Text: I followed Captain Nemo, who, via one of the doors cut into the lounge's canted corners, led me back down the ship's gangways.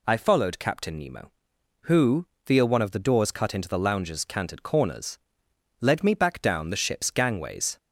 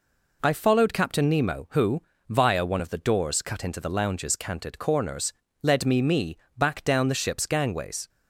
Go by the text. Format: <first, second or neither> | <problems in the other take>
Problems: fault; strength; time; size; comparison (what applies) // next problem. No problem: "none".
first | says "me" twice; at 6.0 s